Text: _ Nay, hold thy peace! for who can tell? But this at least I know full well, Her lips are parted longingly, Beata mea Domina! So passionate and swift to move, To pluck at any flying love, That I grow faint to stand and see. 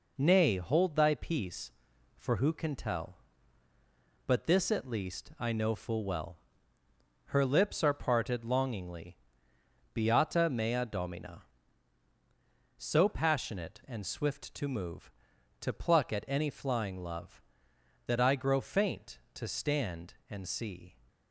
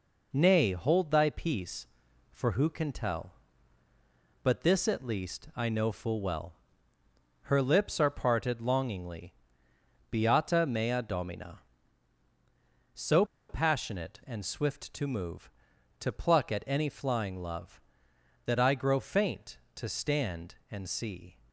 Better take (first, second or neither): first